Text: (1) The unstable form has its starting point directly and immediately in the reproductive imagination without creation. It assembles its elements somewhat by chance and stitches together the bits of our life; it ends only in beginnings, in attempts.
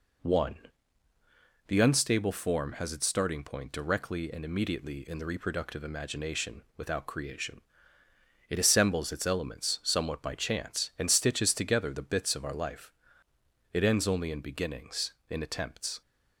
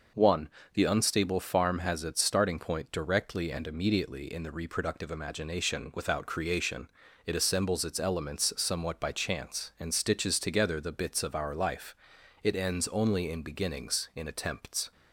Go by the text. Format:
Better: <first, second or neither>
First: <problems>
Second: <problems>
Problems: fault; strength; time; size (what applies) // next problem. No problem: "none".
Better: first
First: none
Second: says "farm" for "form"; at 1.3 s